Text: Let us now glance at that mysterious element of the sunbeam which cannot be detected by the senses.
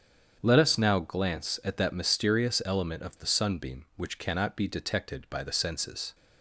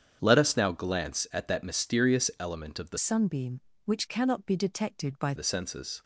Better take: first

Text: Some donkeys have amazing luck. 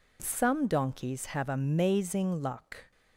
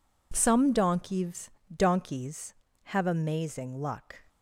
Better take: first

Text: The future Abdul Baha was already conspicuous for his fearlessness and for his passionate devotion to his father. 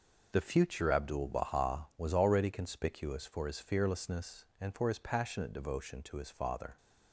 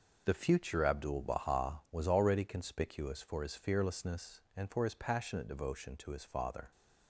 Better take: neither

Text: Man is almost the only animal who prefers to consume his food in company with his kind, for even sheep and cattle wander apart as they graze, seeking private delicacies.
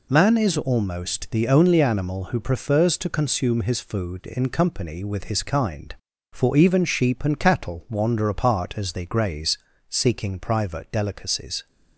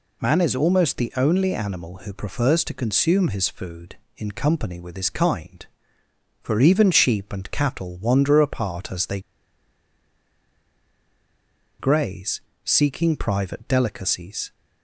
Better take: first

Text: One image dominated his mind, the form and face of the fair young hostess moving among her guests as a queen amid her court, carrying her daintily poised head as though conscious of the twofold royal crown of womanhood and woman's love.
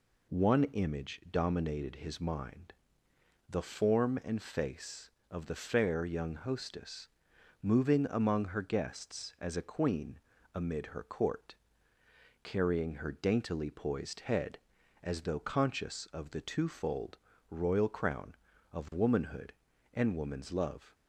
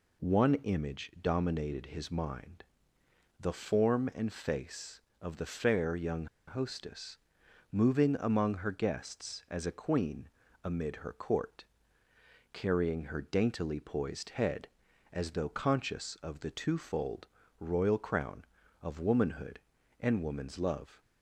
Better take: first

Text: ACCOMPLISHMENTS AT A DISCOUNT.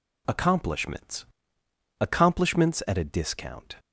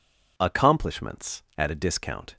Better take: second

